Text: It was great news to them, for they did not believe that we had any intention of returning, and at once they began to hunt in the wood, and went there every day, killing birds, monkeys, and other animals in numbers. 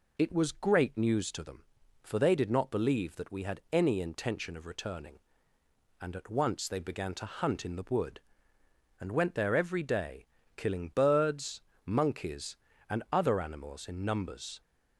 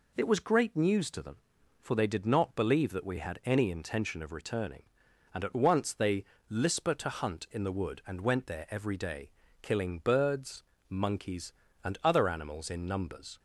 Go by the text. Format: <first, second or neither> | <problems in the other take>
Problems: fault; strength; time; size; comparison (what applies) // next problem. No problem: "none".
first | says "lisper" for "began"; at 6.5 s